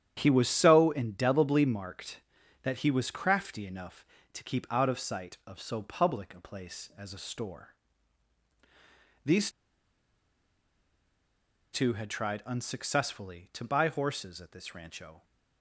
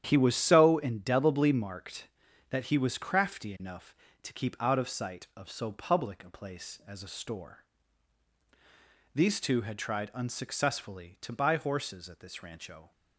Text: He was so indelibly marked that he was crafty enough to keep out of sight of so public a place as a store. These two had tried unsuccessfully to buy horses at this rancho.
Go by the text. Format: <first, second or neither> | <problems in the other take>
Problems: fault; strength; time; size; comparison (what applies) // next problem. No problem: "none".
second | starts louder than the rest; strong; until 1.1 s; 10 dB; strong in the second // pauses between "These" and "two"; strong; at 9.5 s; 2.2 s long